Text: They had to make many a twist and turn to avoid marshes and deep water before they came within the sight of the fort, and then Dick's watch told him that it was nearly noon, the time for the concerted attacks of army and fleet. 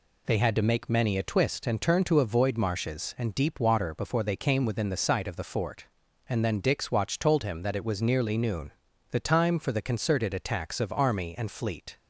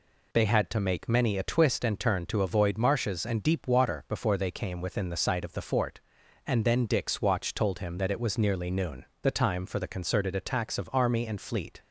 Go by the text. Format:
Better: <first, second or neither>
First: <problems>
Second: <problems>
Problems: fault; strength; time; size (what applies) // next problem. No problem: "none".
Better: neither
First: none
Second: none